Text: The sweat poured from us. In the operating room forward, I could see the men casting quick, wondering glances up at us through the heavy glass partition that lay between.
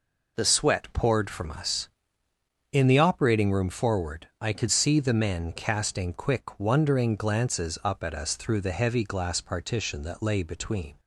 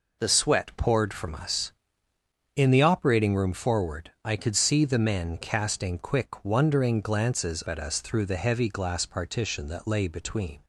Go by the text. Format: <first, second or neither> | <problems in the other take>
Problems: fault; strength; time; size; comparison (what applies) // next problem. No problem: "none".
first | skips "up"; at 7.6 s